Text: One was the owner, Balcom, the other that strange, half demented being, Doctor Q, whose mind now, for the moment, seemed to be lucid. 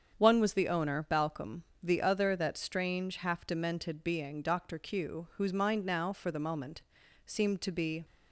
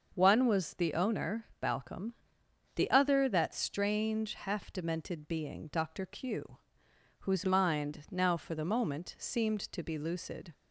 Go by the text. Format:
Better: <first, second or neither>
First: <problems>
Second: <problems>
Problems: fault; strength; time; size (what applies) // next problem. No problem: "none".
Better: second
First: starts louder than the rest; strong; until 1.1 s; 7.5 dB // stops before "lucid"; at 8.0 s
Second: starts louder than the rest; until 1.1 s; 6 dB